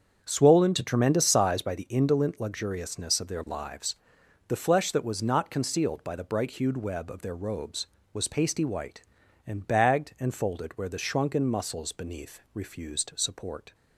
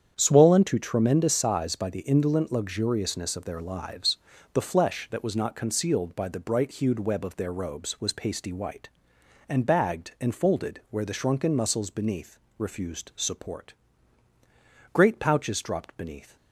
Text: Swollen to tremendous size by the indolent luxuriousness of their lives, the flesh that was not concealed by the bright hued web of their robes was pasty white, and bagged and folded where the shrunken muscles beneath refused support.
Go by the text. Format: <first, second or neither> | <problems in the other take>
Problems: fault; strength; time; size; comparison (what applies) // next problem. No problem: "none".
first | starts louder than the rest; strong; until 1.1 s; 8.5 dB; strong in the first // pauses between "beneath" and "refused"; slight; at 12.3 s; 0.20 s long // goes on to say "Great pouches dropped beneath"; from 14.9 s on; 1.4 s long